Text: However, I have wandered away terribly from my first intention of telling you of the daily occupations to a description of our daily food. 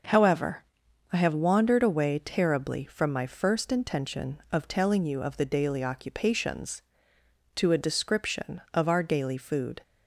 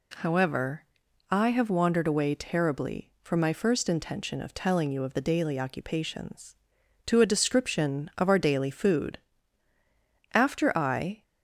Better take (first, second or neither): first